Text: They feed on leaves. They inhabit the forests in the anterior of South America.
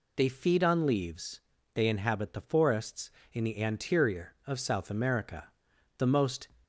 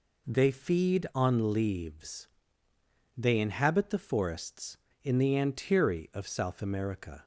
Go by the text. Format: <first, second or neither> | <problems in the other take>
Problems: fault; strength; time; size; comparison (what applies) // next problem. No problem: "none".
second | goes on to say "The most"; from 5.9 s on; 0.52 s long